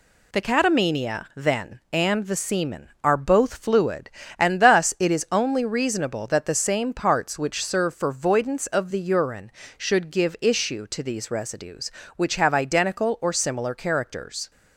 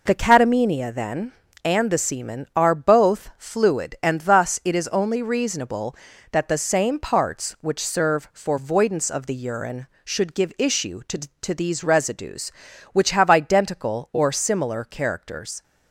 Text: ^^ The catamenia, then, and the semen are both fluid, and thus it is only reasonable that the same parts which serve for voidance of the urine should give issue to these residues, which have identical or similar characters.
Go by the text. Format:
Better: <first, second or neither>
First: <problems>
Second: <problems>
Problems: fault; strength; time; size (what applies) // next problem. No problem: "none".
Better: first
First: none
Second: says "to" twice; at 11.4 s